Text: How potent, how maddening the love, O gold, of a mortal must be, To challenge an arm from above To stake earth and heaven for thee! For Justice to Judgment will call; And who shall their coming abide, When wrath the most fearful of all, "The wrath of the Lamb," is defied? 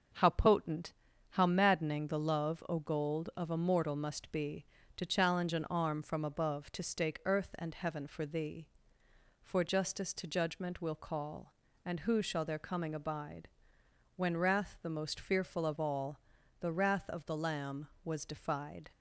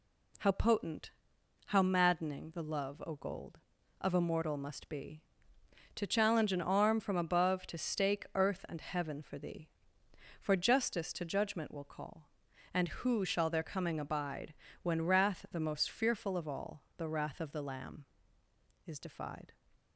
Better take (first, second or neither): second